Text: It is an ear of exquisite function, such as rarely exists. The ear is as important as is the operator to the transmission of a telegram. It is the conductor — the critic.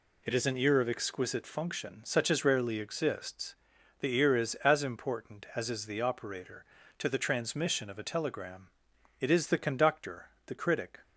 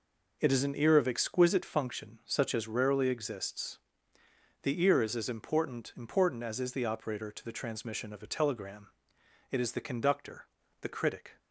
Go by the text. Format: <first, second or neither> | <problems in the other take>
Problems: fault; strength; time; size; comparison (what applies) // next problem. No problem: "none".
first | says "important" twice; at 5.9 s